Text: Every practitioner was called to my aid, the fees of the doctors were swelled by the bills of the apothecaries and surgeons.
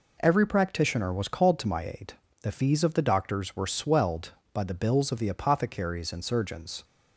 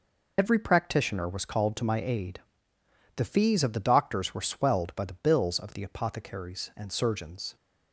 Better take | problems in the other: first | loses the start of "Every"; at 0.3 s; 50 ms

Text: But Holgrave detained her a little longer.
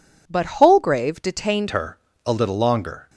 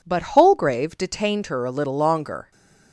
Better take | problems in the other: second | changes voice at "her"; from 1.6 s on; 1.4 s long // pauses between "her" and "a"; slight; at 1.9 s; 0.26 s long

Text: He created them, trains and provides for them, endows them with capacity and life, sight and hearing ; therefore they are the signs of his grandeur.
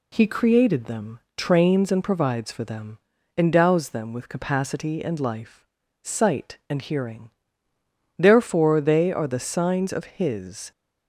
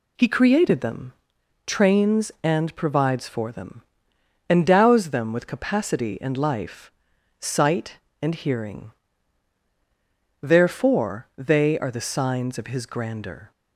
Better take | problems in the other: second | stops before "grandeur"; at 10.7 s

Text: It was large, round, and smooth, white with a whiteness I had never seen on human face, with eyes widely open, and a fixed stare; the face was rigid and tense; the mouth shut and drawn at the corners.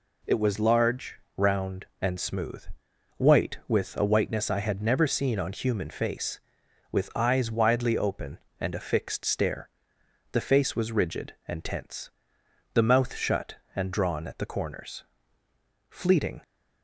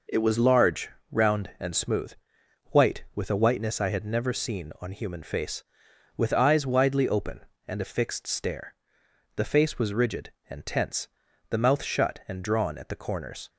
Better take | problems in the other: second | goes on to say "Fleeting"; from 15.8 s on; 0.50 s long

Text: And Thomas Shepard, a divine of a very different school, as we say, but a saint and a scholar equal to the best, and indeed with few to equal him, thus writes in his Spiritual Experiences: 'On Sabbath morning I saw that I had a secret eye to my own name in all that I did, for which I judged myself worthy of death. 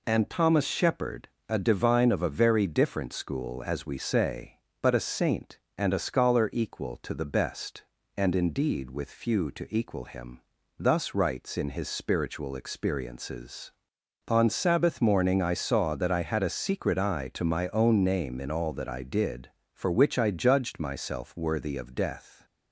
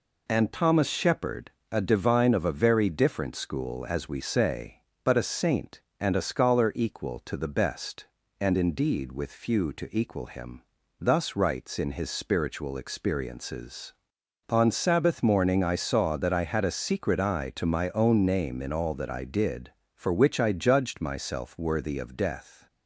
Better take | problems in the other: neither | none

